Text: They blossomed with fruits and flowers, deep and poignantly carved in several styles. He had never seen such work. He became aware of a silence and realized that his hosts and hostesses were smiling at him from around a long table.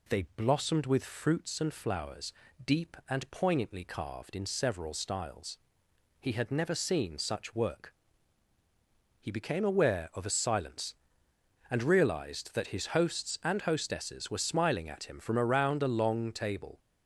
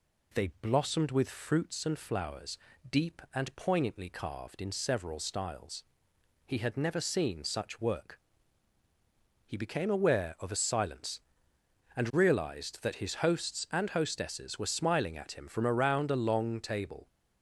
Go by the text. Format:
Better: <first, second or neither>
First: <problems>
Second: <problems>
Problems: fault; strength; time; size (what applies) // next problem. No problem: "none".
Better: neither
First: none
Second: none